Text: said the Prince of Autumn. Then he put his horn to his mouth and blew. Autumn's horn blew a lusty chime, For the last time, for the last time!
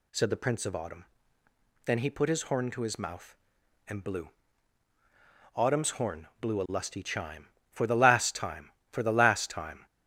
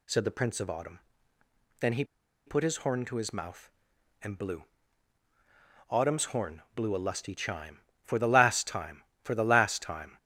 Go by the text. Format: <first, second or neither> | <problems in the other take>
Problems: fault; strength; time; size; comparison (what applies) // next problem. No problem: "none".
first | pauses between "he" and "put"; at 2.0 s; 0.42 s long